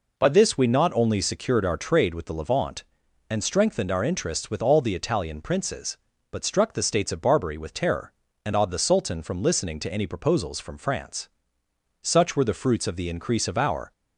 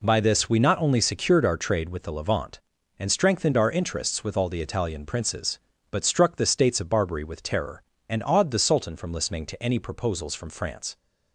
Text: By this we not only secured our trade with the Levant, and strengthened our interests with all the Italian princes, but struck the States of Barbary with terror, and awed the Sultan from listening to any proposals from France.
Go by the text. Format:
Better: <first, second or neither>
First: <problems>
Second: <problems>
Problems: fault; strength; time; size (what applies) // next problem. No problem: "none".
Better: second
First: goes on to say "Such were the fruits of the increase of our"; strong; from 12.0 s on; 1.9 s long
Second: none